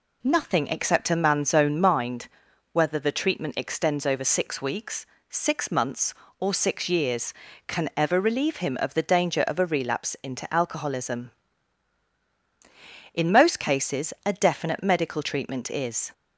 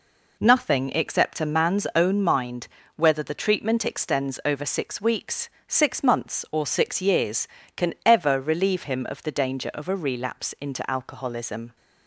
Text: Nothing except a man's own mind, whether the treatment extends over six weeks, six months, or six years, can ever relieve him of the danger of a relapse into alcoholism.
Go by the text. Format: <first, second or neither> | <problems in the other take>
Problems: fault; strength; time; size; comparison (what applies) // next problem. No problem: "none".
second | goes on to say "In most cases a definite medical treatment is"; strong; from 13.1 s on; 2.9 s long